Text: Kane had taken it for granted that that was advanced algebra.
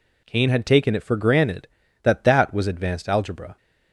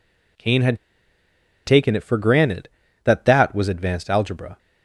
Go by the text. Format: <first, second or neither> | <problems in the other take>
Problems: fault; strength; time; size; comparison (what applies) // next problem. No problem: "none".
first | pauses between "had" and "taken"; noticeable; at 0.7 s; 0.87 s long